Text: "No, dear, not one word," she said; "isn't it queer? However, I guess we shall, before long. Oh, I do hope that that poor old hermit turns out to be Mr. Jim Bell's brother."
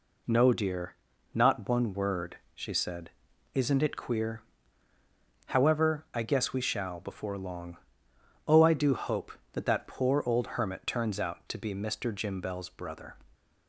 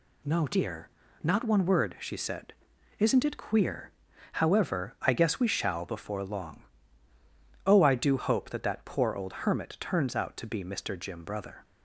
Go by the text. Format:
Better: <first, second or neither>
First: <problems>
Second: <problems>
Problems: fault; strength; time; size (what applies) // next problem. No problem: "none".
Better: first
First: none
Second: skips "Bell's"; at 11.2 s